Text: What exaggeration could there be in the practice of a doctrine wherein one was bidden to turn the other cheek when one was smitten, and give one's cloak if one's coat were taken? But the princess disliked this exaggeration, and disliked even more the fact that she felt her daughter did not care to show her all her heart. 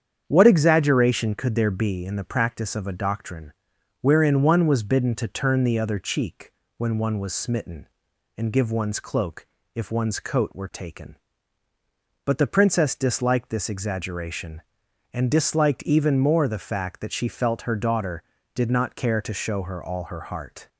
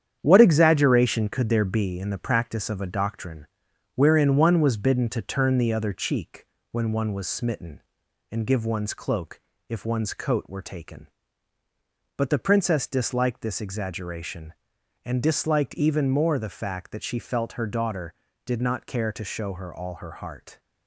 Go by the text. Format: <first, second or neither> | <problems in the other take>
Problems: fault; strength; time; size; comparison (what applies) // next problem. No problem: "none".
first | gets quieter; noticeable; throughout; 5.5 dB // starts louder than the rest; strong; until 1.2 s; 9 dB; strong in the first // pauses between "doctrine" and "wherein"; noticeable; at 3.4 s; 0.48 s long; noticeable in the first // pauses between "cheek" and "when"; slight; at 6.4 s; 0.26 s long; slight in the first // pauses between "cloak" and "if"; slight; at 9.3 s; 0.28 s long; slight in the first